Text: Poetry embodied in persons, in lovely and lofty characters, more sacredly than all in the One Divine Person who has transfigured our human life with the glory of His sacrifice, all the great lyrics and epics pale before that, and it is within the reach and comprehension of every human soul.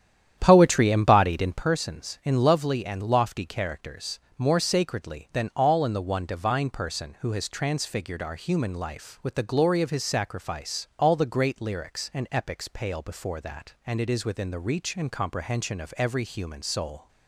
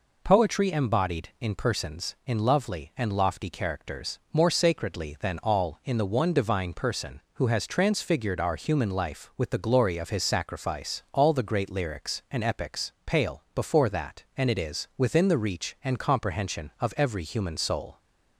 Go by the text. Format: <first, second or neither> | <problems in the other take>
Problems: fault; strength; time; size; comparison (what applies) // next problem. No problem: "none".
second | starts louder than the rest; strong; until 1.7 s; 10 dB